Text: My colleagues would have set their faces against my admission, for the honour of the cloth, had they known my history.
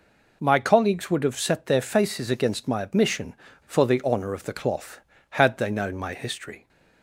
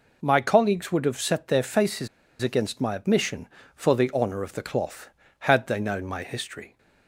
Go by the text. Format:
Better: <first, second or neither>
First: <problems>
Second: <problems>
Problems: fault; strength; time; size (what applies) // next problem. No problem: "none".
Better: first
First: none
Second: pauses between "faces" and "against"; slight; at 2.0 s; 0.33 s long